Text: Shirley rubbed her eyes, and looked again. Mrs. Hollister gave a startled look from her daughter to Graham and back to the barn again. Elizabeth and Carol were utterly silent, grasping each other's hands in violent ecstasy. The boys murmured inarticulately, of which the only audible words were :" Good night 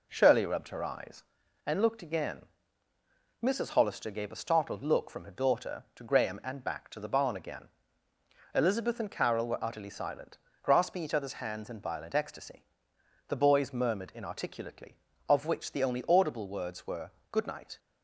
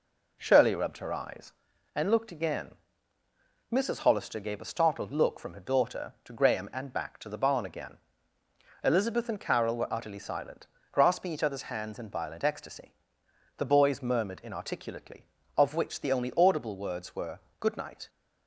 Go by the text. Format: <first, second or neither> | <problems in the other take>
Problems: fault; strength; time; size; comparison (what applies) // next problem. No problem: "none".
neither | none